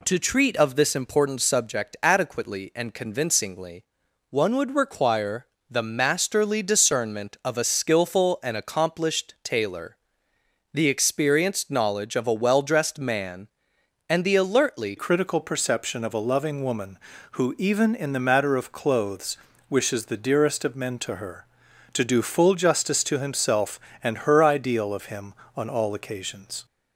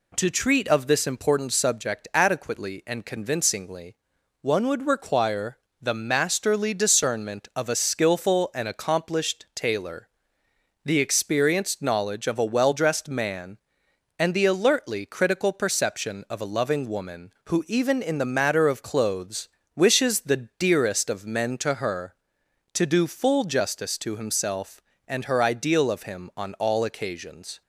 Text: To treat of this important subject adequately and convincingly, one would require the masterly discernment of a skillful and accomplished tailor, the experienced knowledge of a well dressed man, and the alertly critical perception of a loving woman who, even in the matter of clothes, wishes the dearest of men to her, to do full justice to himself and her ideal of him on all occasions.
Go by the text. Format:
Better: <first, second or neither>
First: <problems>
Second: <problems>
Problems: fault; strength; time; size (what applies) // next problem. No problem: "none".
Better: second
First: pauses between "require" and "the"; slight; at 5.4 s; 0.24 s long // changes voice at "critical"; from 14.9 s on; 11.7 s long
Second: pauses between "require" and "the"; slight; at 5.5 s; 0.24 s long